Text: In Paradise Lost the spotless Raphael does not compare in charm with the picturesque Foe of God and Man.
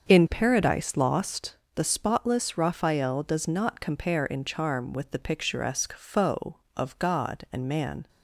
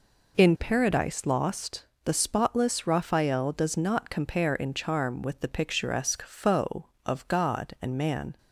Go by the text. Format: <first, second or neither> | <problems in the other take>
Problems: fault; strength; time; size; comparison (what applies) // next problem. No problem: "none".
second | starts louder than the rest; until 1.8 s; 7 dB // pauses between "Lost" and "the"; slight; at 1.5 s; 0.22 s long; slight in the second